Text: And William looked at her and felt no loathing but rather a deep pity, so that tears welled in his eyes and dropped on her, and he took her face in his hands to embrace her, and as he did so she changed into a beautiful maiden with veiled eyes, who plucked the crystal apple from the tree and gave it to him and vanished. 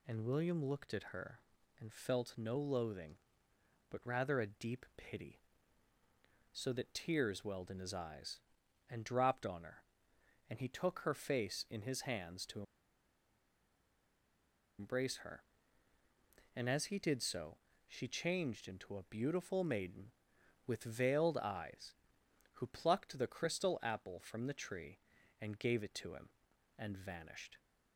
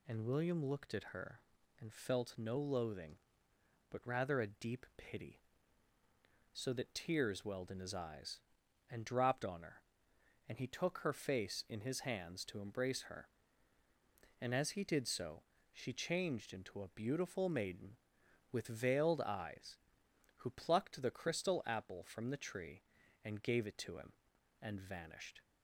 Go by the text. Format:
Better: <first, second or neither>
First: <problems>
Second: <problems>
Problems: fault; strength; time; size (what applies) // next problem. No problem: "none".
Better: second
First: pauses between "to" and "embrace"; strong; at 12.6 s; 2.1 s long // pauses between "so" and "she"; slight; at 17.5 s; 0.30 s long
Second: pauses between "so" and "she"; slight; at 15.4 s; 0.30 s long